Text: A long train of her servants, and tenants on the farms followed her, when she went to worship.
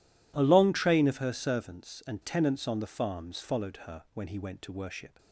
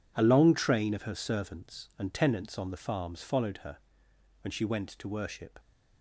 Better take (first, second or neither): second